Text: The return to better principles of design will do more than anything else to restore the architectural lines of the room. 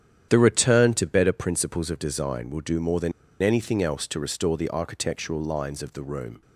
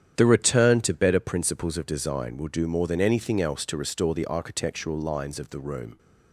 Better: second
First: starts louder than the rest; strong; until 1.3 s; 9.5 dB // pauses between "than" and "anything"; slight; at 3.1 s; 0.31 s long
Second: starts louder than the rest; strong; until 1.1 s; 9.5 dB

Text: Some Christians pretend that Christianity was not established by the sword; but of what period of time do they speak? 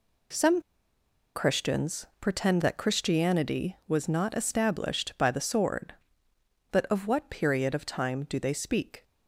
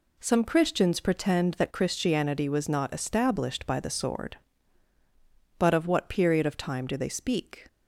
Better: second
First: pauses between "Some" and "Christians"; noticeable; at 0.6 s; 0.73 s long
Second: none

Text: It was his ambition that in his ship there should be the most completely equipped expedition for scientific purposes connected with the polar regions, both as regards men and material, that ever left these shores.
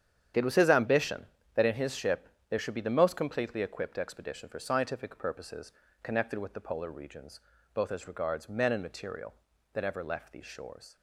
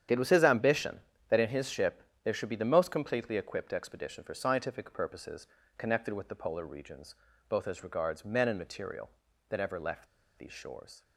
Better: first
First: starts louder than the rest; strong; until 1.6 s; 9 dB // pauses between "ship" and "there"; slight; at 2.2 s; 0.22 s long // pauses between "purposes" and "connected"; slight; at 5.7 s; 0.32 s long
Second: starts louder than the rest; strong; until 1.3 s; 9 dB // pauses between "ship" and "there"; slight; at 2.0 s; 0.22 s long // pauses between "purposes" and "connected"; slight; at 5.4 s; 0.32 s long // pauses between "left" and "these"; slight; at 10.0 s; 0.31 s long

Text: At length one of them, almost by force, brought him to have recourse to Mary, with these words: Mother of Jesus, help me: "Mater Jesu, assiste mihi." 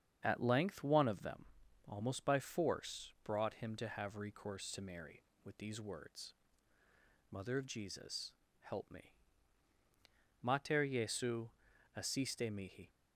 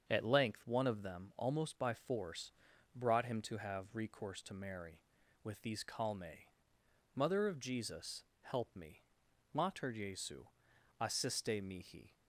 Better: first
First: starts louder than the rest; strong; until 1.2 s; 8 dB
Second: starts louder than the rest; until 1.0 s; 6.5 dB // says "calme" for "words"; at 5.8 s

